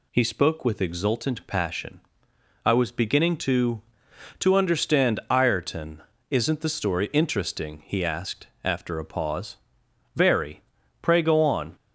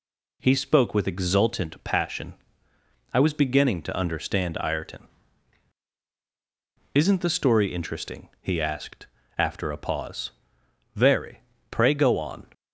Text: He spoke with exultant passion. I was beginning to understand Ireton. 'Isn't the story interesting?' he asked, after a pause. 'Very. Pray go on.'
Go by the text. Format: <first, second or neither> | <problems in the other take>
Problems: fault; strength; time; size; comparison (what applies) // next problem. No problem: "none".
second | says "to" twice; at 4.3 s